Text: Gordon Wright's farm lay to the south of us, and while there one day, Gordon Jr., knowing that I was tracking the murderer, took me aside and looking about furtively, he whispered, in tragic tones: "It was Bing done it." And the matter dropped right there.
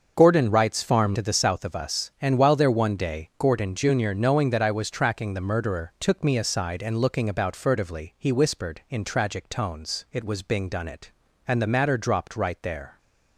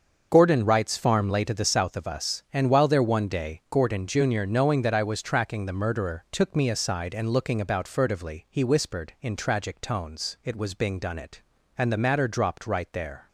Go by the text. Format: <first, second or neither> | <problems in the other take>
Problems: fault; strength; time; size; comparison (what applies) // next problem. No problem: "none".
second | starts louder than the rest; until 1.1 s; 6.5 dB; also in the second // skips "lay"; at 1.1 s